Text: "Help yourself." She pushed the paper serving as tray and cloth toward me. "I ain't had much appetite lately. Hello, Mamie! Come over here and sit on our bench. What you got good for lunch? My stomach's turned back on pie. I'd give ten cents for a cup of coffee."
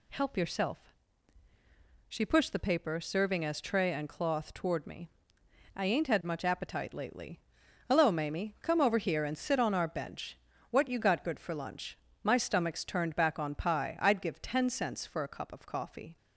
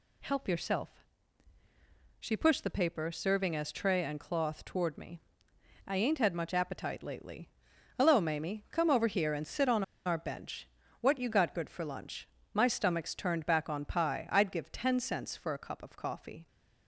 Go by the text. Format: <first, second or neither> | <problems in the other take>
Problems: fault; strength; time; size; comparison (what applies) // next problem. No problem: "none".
first | pauses between "on" and "our"; slight; at 9.8 s; 0.22 s long